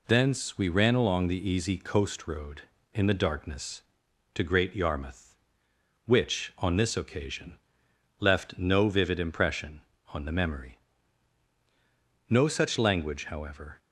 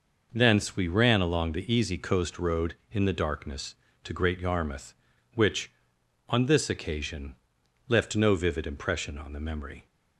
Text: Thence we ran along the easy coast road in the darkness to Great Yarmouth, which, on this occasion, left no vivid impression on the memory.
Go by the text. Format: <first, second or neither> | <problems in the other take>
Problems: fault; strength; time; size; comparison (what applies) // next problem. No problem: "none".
second | goes on to say "No such language however"; from 12.3 s on; 1.4 s long